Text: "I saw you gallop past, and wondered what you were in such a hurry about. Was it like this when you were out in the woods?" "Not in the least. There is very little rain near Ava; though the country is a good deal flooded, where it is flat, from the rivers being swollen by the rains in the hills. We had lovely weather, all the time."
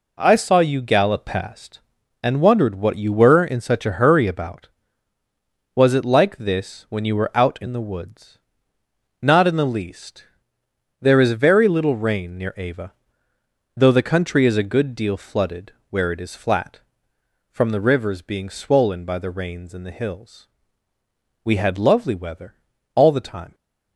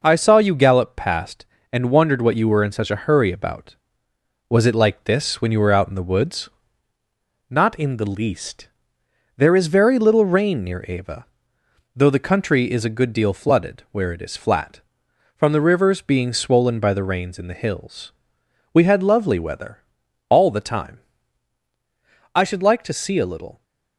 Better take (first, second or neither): first